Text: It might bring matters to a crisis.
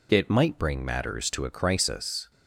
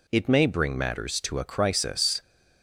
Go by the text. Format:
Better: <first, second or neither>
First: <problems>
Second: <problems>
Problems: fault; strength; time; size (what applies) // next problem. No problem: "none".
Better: first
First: none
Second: says "may" for "might"; at 0.2 s